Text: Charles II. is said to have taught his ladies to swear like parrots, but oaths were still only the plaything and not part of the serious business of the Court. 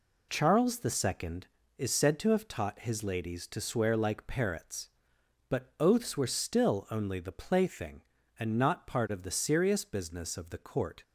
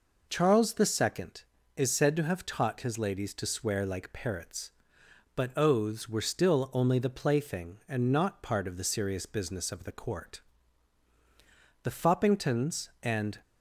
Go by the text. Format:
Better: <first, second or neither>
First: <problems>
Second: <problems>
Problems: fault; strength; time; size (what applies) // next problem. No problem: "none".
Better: first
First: none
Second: goes on to say "The Foppingtons and"; from 11.8 s on; 1.5 s long